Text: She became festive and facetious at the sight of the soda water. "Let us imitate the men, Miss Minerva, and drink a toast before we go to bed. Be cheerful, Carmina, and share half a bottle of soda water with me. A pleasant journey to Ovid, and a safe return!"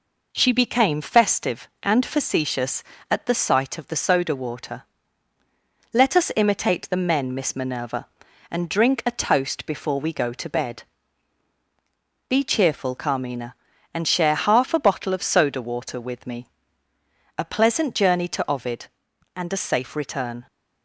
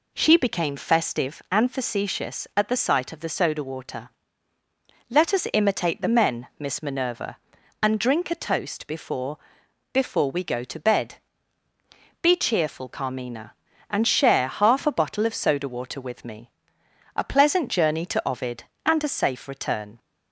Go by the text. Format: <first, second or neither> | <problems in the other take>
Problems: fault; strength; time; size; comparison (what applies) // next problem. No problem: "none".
first | says "before" twice; at 9.9 s